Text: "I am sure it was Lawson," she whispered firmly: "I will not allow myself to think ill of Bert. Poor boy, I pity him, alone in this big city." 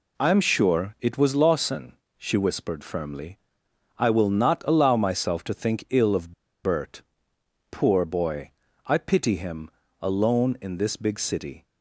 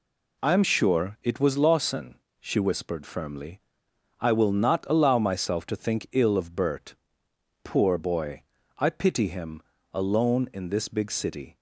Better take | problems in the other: second | pauses between "of" and "Bert"; slight; at 6.3 s; 0.32 s long

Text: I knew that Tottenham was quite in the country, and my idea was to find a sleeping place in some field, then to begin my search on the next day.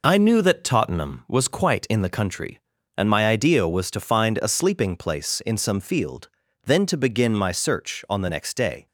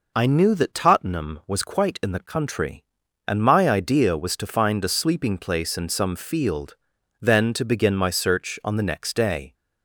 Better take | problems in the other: neither | none

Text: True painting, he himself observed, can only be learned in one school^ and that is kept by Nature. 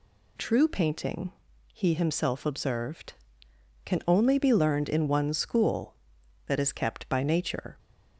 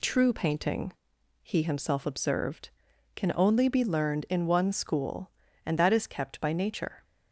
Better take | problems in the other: second | skips "and"; at 6.1 s

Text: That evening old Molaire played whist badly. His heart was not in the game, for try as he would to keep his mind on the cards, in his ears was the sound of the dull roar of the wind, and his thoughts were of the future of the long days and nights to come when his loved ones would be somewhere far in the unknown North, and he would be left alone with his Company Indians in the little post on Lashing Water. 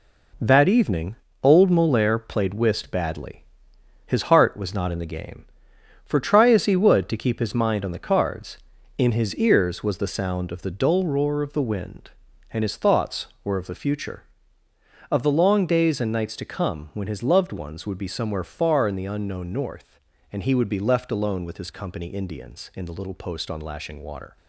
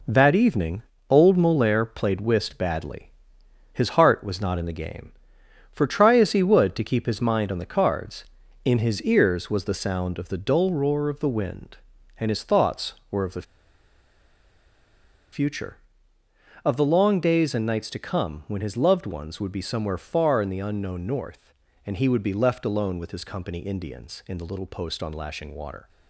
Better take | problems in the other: first | pauses between "evening" and "old"; slight; at 0.8 s; 0.30 s long; slight in the first // pauses between "the" and "future"; strong; at 13.4 s; 1.8 s long

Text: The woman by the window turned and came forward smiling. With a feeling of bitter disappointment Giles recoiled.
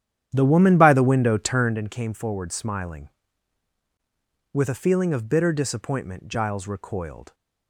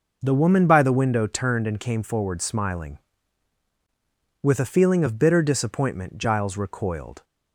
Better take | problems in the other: second | starts louder than the rest; strong; until 1.8 s; 10 dB

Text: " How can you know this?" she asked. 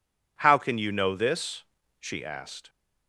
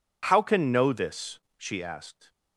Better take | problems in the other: first | skips "you"; at 0.7 s

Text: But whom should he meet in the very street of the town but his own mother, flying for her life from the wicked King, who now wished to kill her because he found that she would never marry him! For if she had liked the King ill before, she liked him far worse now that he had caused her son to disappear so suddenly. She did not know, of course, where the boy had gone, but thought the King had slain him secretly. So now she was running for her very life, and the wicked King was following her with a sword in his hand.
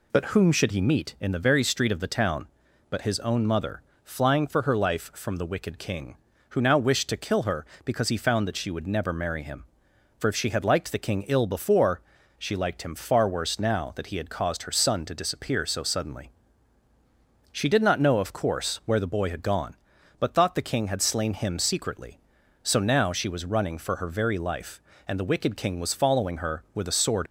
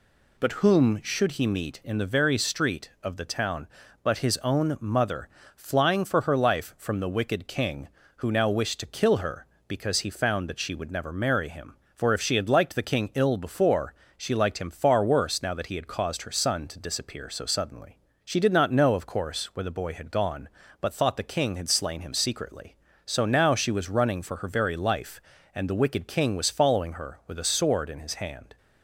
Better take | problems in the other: second | stops before "in his hand"; at 27.2 s

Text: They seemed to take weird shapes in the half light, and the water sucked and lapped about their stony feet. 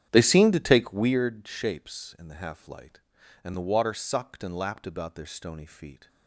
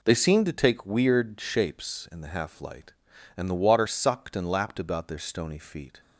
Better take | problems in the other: second | starts louder than the rest; strong; until 1.2 s; 9.5 dB

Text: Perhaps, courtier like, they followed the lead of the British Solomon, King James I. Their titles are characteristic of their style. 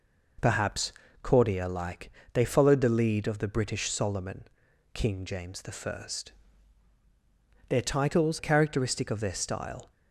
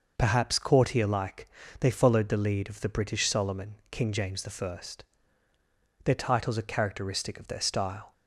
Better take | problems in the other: second | skips "are"; at 8.3 s

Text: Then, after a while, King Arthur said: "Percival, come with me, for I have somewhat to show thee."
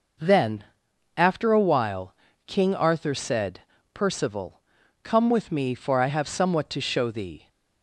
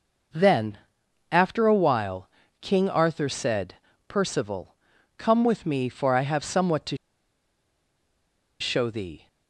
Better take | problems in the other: first | pauses between "to" and "show"; strong; at 6.9 s; 1.6 s long

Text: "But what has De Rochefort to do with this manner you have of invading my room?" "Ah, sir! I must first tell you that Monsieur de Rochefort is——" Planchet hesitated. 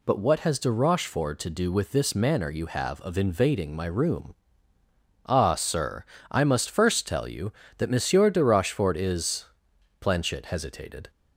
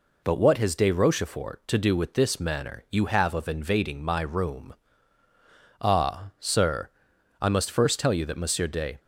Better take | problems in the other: first | stops before "Rochefort is Planchet hesitated"; at 8.9 s

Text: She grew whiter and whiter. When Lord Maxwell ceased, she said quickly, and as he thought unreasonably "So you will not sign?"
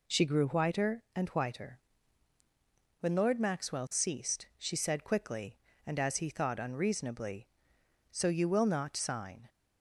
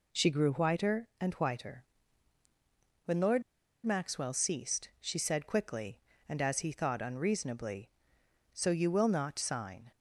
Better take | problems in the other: first | pauses between "Lord" and "Maxwell"; at 3.4 s; 0.42 s long

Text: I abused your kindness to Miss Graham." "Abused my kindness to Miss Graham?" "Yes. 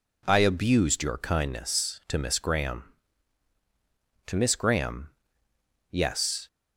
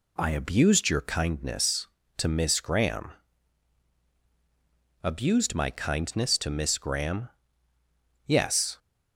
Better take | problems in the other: second | skips "Abused my kindness"; at 3.5 s

